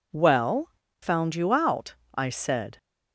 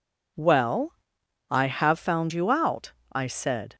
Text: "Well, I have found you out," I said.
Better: second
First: skips "I have"; at 0.8 s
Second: none

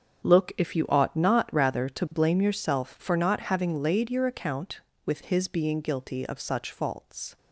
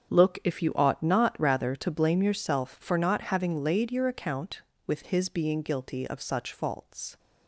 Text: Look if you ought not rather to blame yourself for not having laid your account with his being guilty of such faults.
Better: neither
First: starts louder than the rest; strong; until 1.2 s; 7.5 dB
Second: starts louder than the rest; strong; until 1.1 s; 8 dB

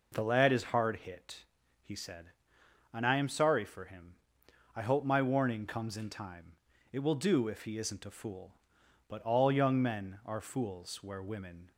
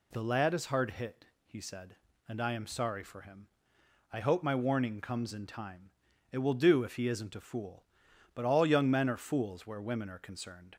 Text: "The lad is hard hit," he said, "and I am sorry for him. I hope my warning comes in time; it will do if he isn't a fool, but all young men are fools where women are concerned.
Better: second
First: stops before "are concerned"; at 11.7 s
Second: none

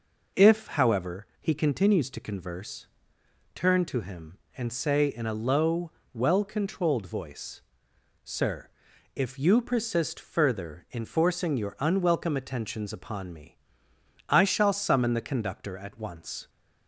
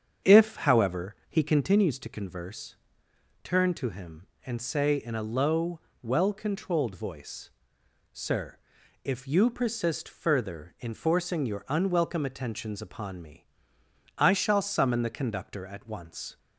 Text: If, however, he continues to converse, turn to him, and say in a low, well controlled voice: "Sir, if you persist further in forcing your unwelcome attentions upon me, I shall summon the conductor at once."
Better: first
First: none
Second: starts louder than the rest; strong; until 1.8 s; 7.5 dB

